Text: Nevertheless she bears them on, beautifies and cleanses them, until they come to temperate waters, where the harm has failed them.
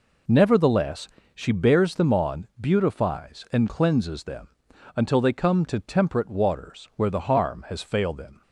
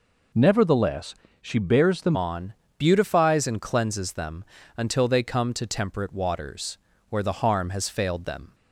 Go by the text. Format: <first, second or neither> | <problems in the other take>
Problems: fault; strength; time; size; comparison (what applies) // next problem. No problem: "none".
first | pauses between "Nevertheless" and "she"; slight; at 1.1 s; 0.28 s long; slight in the first // changes voice at "on"; from 2.1 s on; 6.4 s long